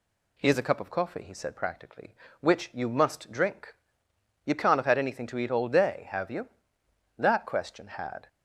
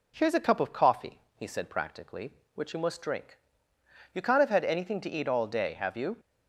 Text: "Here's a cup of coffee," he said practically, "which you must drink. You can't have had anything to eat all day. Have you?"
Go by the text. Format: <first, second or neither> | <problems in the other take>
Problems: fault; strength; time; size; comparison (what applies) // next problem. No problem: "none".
second | goes on to say "That question had"; noticeable; from 7.1 s on; 1.1 s long